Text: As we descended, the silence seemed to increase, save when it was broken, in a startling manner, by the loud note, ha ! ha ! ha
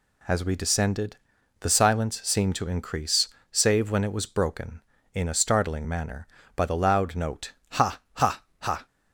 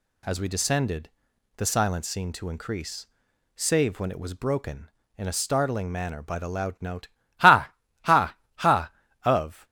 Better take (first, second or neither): first